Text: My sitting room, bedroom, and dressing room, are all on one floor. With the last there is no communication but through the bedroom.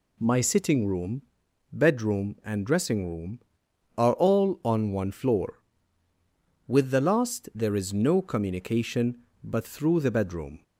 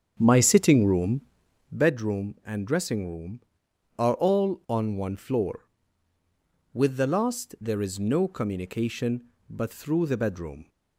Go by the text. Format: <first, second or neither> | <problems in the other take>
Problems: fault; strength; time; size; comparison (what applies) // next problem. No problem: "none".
first | starts louder than the rest; strong; until 1.9 s; 8 dB